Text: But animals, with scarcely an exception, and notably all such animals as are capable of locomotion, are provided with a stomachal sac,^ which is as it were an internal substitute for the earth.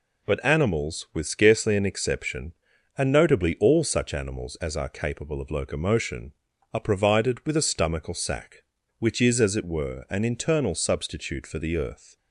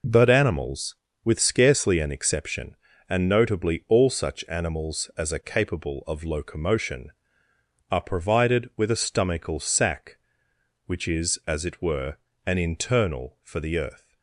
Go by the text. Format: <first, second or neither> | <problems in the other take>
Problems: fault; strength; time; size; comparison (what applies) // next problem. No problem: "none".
first | pauses between "were" and "an"; slight; at 12.1 s; 0.32 s long // skips "substitute"; at 13.3 s